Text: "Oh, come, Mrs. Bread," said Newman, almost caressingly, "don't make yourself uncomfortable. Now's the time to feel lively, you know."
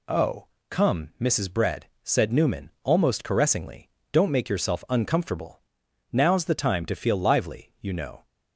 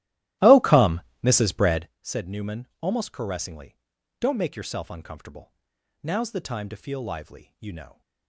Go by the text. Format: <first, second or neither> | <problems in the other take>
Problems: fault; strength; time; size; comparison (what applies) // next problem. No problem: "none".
first | starts louder than the rest; strong; until 1.9 s; 15.5 dB